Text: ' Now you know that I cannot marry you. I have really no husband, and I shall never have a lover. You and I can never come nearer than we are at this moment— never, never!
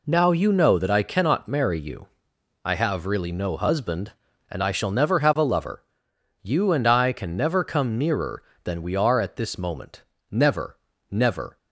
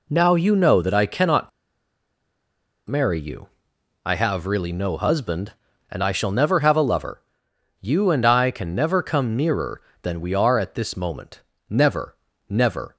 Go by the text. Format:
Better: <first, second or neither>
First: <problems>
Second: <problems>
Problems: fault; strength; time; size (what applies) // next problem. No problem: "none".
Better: first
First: none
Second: pauses between "cannot" and "marry"; strong; at 1.4 s; 1.3 s long